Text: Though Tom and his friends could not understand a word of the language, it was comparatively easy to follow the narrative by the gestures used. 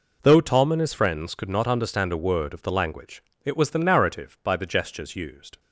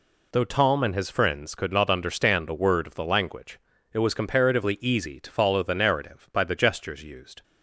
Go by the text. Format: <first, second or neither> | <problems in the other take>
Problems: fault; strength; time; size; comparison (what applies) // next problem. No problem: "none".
second | skips "comparatively easy to follow"; at 3.6 s